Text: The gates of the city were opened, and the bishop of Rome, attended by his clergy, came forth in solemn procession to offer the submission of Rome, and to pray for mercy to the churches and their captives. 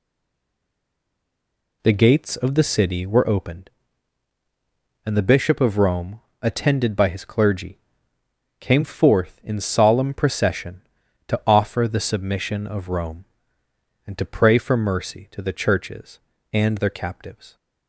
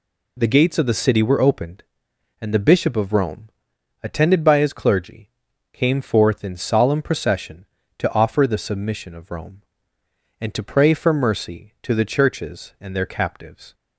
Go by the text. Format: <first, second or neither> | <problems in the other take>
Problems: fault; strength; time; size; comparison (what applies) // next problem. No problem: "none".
second | stays silent before the first word; noticeable; until 1.8 s; 1.8 s long